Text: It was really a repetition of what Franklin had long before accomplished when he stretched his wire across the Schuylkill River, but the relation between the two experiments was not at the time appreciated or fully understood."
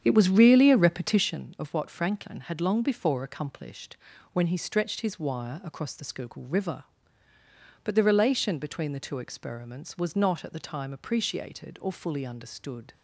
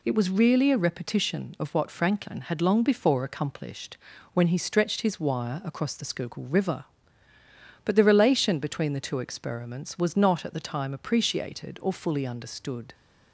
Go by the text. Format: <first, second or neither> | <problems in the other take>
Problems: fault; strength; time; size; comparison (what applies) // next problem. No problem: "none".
second | starts louder than the rest; strong; until 1.4 s; 8.5 dB // pauses between "accomplished" and "when"; slight; at 3.9 s; 0.36 s long; slight in the second